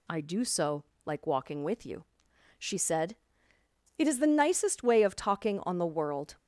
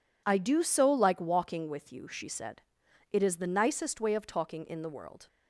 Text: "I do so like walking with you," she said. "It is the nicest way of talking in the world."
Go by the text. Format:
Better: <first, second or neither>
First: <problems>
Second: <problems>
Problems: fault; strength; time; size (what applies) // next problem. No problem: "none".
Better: second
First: pauses between "so" and "like"; slight; at 0.8 s; 0.20 s long // says "on" for "in"; at 5.6 s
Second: none